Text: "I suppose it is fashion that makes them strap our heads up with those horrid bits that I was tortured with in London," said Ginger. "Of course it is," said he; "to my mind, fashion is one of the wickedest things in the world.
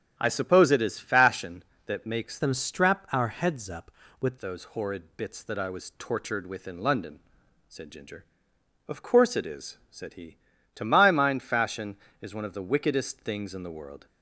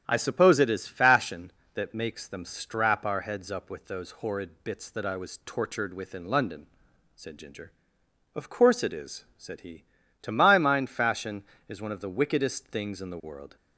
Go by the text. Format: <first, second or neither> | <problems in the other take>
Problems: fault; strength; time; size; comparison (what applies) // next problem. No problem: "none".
second | starts louder than the rest; strong; until 1.1 s; 8.5 dB; strong in the second // changes voice from "them" to "with"; from 2.3 to 4.3 s; 2.0 s long